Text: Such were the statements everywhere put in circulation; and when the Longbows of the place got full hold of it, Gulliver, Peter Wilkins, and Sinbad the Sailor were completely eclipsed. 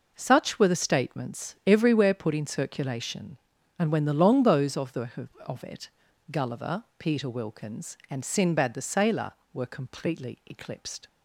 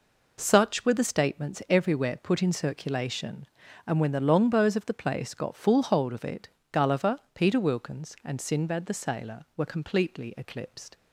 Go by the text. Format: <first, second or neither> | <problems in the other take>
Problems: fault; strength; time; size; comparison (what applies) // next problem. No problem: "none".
second | skips "place got full hold"; at 5.3 s